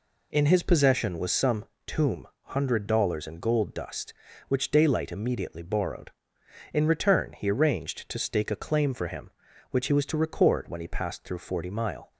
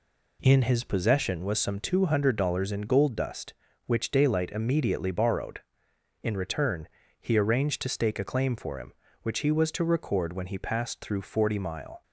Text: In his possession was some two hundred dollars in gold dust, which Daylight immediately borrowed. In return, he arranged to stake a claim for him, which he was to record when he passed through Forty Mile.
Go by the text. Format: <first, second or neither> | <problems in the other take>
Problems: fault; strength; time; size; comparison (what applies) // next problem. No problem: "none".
second | says "tomb" for "two"; at 1.8 s